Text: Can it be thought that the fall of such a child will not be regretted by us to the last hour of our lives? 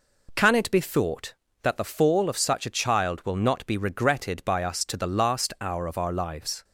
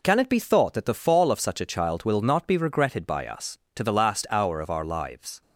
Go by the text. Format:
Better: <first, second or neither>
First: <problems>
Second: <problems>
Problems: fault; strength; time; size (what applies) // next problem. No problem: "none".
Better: neither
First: none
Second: none